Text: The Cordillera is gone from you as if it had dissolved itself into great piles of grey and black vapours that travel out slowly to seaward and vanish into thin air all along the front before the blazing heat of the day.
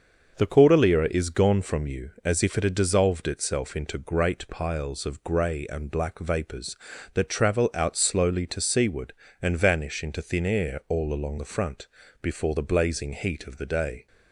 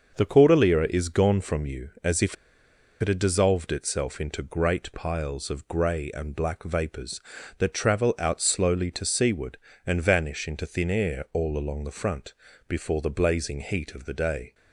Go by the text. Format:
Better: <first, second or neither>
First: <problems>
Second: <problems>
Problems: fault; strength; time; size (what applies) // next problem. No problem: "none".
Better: first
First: starts louder than the rest; until 1.4 s; 6.5 dB // pauses between "front" and "before"; slight; at 11.8 s; 0.36 s long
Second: starts louder than the rest; until 1.2 s; 6.5 dB // pauses between "if" and "it"; noticeable; at 2.3 s; 0.67 s long // pauses between "front" and "before"; slight; at 12.3 s; 0.36 s long